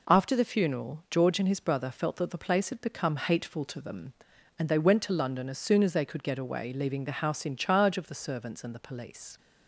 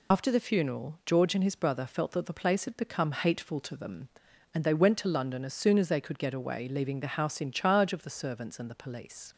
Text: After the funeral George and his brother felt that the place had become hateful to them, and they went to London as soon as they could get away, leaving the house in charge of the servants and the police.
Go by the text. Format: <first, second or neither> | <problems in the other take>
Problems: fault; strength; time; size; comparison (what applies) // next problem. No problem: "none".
first | loses the start of "After"; at 0.1 s; 80 ms